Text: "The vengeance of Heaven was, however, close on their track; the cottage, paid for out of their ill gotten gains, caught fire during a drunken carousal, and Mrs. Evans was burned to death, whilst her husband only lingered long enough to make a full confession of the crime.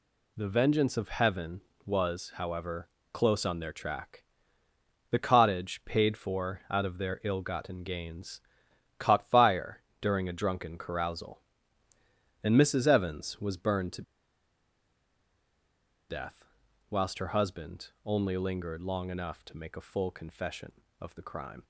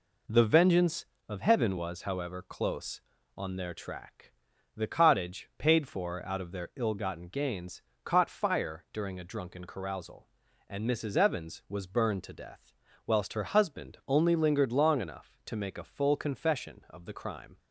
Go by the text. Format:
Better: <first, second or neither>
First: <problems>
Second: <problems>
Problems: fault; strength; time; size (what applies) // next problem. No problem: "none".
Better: second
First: pauses between "fire" and "during"; slight; at 9.8 s; 0.16 s long // pauses between "to" and "death"; strong; at 14.0 s; 2.0 s long // pauses between "husband" and "only"; slight; at 17.8 s; 0.16 s long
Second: none